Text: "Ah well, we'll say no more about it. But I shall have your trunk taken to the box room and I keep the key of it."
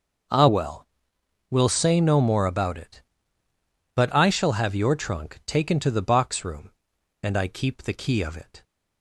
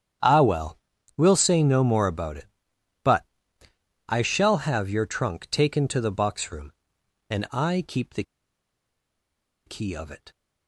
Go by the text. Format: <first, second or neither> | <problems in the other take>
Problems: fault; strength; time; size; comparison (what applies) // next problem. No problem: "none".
first | starts louder than the rest; strong; until 1.5 s; 9 dB; also in the first // pauses between "But" and "I"; noticeable; at 3.2 s; 0.82 s long // pauses between "the" and "key"; strong; at 8.2 s; 1.4 s long